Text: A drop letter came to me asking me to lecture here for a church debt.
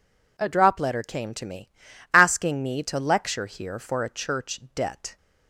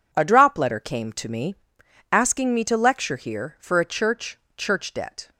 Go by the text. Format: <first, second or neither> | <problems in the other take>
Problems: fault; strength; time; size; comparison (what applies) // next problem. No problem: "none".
first | pauses between "me" and "asking"; noticeable; at 1.5 s; 0.58 s long; also in the first // says "church" twice; at 4.5 s